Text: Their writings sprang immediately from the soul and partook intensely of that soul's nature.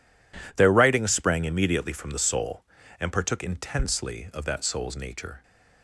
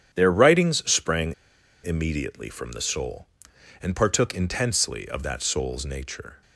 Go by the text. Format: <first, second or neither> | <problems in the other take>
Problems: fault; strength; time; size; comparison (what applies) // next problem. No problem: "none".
first | starts louder than the rest; strong; until 1.1 s; 9.5 dB // pauses between "sprang" and "immediately"; noticeable; at 1.3 s; 0.51 s long